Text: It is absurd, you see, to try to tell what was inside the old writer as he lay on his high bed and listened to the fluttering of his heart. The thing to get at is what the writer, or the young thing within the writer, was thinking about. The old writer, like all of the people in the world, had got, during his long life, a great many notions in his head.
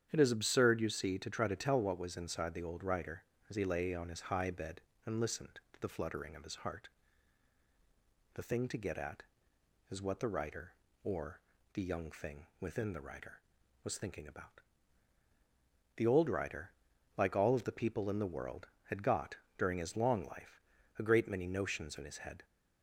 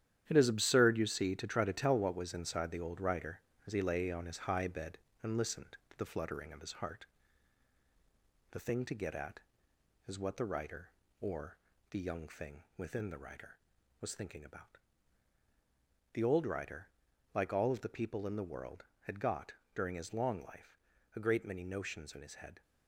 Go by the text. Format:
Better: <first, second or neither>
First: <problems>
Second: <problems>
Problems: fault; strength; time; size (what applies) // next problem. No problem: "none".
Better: first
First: starts louder than the rest; strong; until 1.1 s; 9 dB // pauses between "or" and "the"; slight; at 11.4 s; 0.34 s long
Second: gets quieter; strong; throughout; 8 dB // starts louder than the rest; strong; until 1.2 s; 10.5 dB // pauses between "or" and "the"; slight; at 11.5 s; 0.34 s long